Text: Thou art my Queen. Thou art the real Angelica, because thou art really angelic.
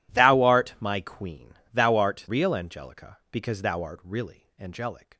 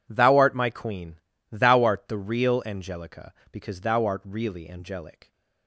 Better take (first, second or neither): second